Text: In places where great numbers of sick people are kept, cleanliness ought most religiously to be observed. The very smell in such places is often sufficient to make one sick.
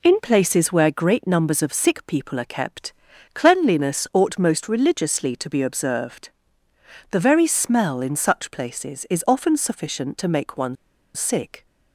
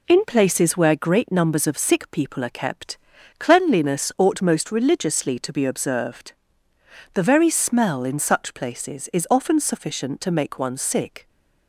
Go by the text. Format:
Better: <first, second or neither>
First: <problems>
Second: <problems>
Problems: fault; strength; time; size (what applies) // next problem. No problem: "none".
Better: second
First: pauses between "one" and "sick"; at 10.7 s; 0.40 s long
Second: none